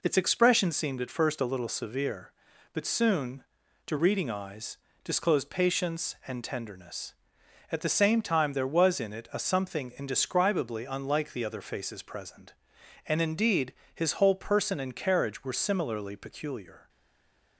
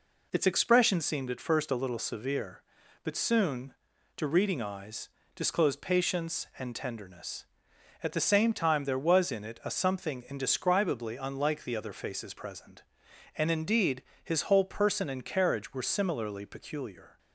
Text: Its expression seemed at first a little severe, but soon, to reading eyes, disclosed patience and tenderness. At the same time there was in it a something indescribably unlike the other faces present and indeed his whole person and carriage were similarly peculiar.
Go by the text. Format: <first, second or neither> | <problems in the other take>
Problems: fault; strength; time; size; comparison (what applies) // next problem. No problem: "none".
second | pauses between "indeed" and "his"; slight; at 13.7 s; 0.22 s long; slight in the second // stays silent after the last word; slight; from 16.8 s on; 0.7 s long